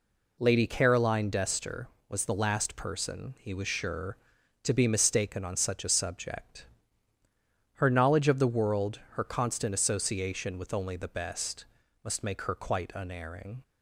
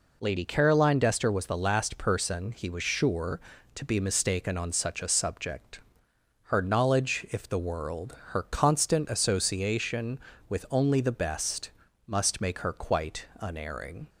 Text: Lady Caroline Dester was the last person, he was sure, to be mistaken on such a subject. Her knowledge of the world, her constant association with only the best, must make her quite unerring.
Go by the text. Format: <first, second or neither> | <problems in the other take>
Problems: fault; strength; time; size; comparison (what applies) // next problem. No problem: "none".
first | says "if" for "of"; at 7.3 s // pauses between "quite" and "unerring"; slight; at 13.2 s; 0.16 s long